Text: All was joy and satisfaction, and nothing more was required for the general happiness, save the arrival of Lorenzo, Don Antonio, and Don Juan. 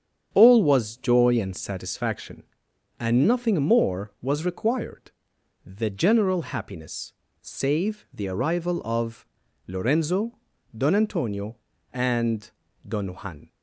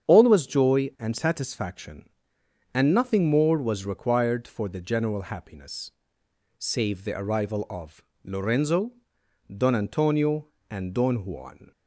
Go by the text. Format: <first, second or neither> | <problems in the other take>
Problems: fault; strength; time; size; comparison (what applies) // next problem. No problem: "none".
second | starts louder than the rest; strong; until 1.3 s; 8 dB; strong in the second // skips "for"; at 5.3 s // pauses between "of" and "Lorenzo"; at 9.2 s; 0.40 s long; slight in the second // pauses between "and" and "Don"; slight; at 12.4 s; 0.36 s long